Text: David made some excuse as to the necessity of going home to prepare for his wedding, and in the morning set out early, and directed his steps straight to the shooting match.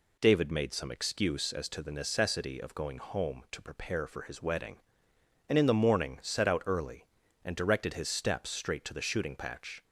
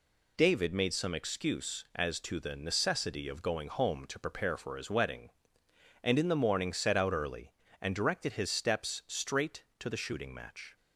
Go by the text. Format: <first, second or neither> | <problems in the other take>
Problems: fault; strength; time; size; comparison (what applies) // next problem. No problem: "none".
second | says "patch" for "match"; at 9.3 s